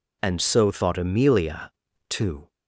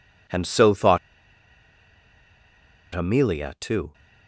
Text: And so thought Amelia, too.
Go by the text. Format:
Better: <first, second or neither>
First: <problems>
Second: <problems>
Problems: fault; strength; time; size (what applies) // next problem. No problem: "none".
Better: first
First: none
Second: pauses between "thought" and "Amelia"; strong; at 0.9 s; 1.9 s long